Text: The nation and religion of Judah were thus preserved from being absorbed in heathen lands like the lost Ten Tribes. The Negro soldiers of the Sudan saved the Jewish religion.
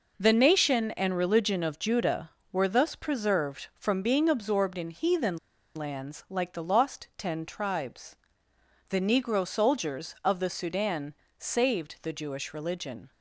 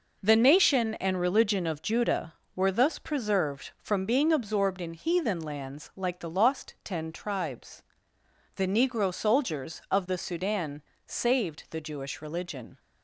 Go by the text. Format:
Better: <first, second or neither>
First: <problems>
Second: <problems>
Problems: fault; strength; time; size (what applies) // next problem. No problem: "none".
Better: second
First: pauses between "heathen" and "lands"; at 5.3 s; 0.39 s long // pauses between "Sudan" and "saved"; slight; at 11.1 s; 0.24 s long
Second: pauses between "Sudan" and "saved"; slight; at 10.8 s; 0.24 s long